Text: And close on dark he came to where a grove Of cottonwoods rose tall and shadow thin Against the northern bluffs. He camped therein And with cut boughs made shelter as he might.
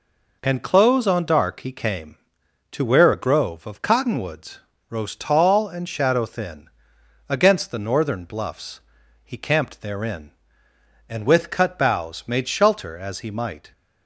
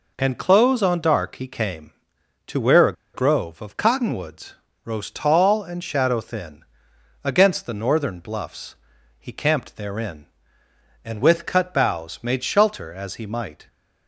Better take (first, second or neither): first